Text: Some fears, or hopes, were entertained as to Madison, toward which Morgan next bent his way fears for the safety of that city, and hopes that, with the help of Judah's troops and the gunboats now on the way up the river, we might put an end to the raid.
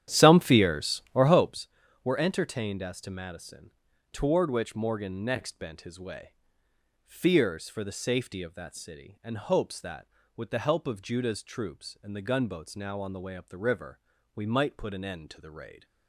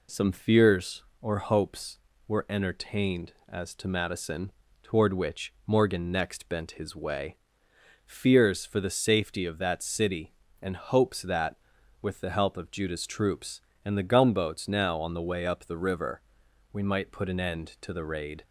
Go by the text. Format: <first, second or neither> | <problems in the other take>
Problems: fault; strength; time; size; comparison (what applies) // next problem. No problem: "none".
second | starts louder than the rest; strong; until 1.6 s; 10.5 dB // pauses between "way" and "fears"; noticeable; at 6.3 s; 0.74 s long; noticeable in the second